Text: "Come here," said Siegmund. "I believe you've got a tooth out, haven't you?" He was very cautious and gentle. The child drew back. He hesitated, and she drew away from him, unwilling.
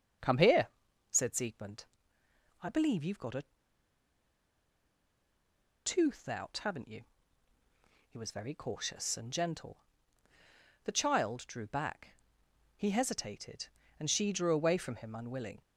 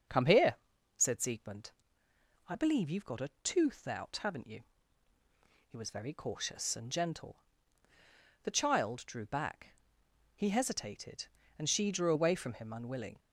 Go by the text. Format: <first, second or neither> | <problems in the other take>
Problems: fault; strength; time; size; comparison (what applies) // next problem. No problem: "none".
second | starts louder than the rest; until 1.6 s; 6.5 dB; also in the second // pauses between "a" and "tooth"; strong; at 3.4 s; 2.3 s long